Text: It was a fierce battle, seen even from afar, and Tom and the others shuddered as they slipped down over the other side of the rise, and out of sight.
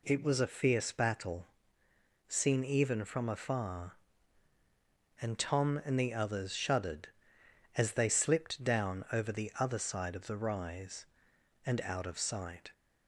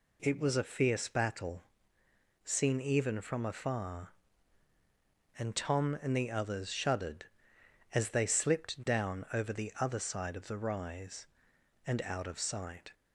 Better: neither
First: none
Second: none

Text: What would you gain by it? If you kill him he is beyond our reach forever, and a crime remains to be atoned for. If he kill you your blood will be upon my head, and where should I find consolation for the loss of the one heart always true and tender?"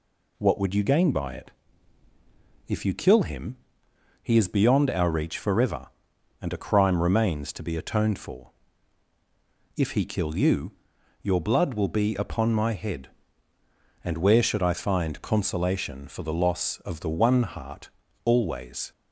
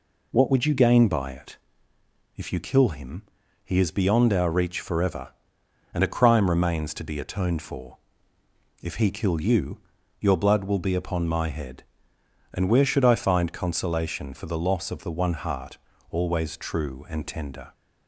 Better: second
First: pauses between "him" and "he"; noticeable; at 3.5 s; 0.64 s long // pauses between "you" and "your"; noticeable; at 10.7 s; 0.48 s long // pauses between "heart" and "always"; slight; at 17.8 s; 0.36 s long // stops before "true and tender"; at 18.9 s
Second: pauses between "him" and "he"; at 3.2 s; 0.42 s long // pauses between "you" and "your"; at 9.7 s; 0.42 s long // pauses between "heart" and "always"; slight; at 15.7 s; 0.34 s long

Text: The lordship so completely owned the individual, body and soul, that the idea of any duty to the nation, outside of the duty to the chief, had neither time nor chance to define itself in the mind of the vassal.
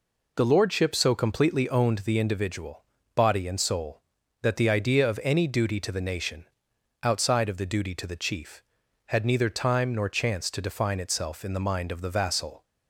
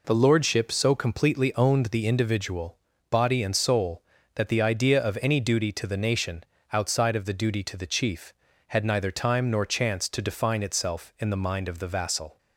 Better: neither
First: none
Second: none

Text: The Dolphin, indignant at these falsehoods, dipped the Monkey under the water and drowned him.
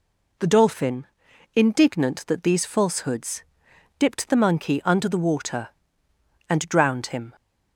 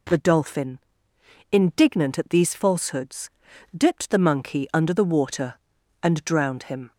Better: second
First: says "that" for "at"; at 2.2 s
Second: none

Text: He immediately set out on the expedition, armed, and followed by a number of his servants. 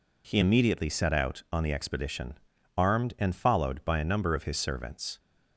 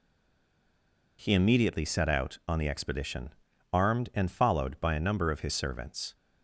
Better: first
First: none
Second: stays silent before the first word; noticeable; until 1.1 s; 1.1 s long

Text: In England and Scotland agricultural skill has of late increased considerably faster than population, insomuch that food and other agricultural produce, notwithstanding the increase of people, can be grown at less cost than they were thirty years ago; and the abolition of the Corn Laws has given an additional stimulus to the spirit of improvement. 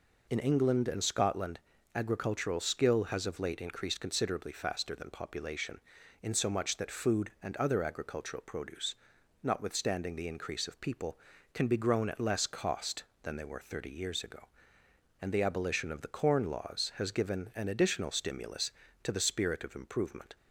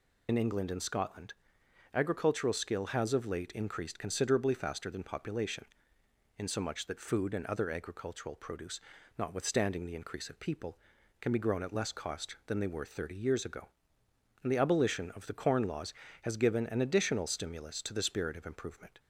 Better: first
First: pauses between "Scotland" and "agricultural"; slight; at 1.5 s; 0.36 s long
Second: loses the start of "In"; at 0.2 s; 65 ms // pauses between "Scotland" and "agricultural"; noticeable; at 1.3 s; 0.60 s long

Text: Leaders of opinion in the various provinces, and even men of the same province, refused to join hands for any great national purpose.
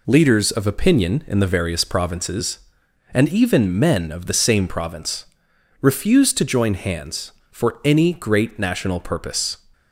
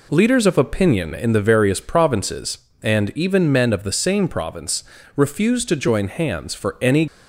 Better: first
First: none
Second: stops before "great national purpose"; at 7.0 s

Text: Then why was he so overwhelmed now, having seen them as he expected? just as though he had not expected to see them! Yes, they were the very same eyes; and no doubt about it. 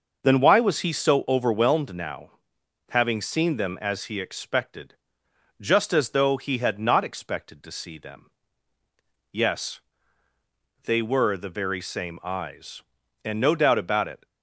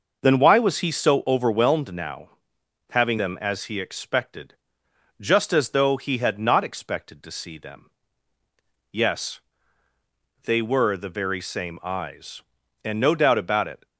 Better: first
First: none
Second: skips "seen"; at 3.1 s

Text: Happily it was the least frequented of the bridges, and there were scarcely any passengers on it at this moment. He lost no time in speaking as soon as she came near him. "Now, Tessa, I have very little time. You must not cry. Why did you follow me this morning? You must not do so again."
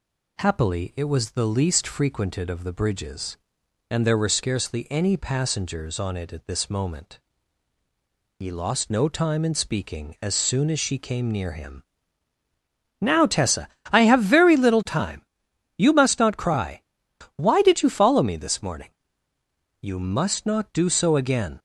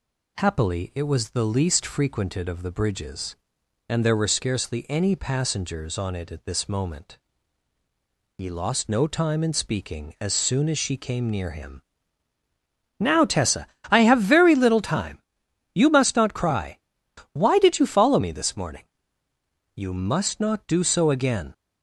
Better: neither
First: none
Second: none

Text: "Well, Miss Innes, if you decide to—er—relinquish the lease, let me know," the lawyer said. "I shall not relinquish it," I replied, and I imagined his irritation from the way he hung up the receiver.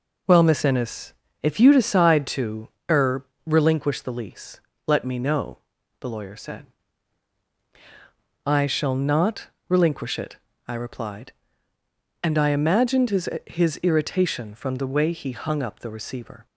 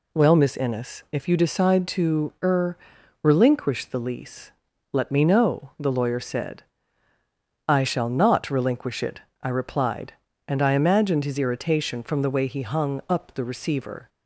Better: second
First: pauses between "not" and "relinquish"; slight; at 9.4 s; 0.18 s long // says "his" twice; at 13.4 s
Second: none

